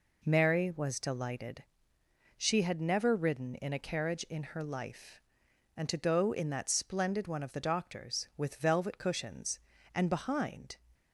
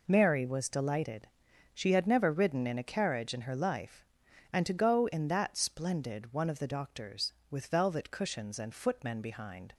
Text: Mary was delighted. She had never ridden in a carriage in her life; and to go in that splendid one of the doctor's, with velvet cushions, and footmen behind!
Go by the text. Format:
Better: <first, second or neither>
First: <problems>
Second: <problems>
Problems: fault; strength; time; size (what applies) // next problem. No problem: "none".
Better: second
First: skips "footmen"; at 10.0 s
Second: none